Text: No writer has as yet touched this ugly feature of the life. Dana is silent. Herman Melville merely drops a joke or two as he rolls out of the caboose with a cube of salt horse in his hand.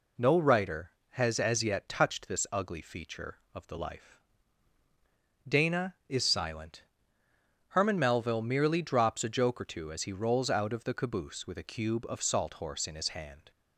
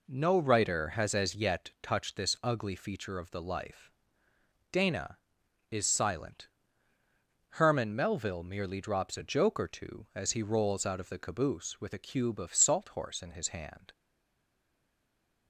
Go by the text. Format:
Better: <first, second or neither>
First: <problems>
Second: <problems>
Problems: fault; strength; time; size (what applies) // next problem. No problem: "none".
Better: first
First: none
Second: stays silent after the last word; noticeable; from 13.9 s on; 1.5 s long